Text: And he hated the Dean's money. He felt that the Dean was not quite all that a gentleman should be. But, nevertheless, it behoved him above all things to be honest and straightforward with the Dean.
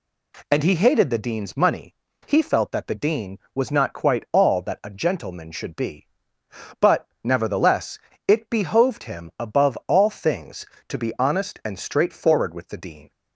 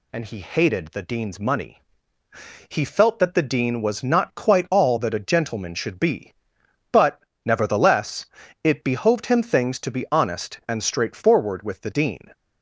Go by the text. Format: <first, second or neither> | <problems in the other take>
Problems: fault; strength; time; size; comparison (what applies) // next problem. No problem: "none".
first | skips "above all"; at 9.4 s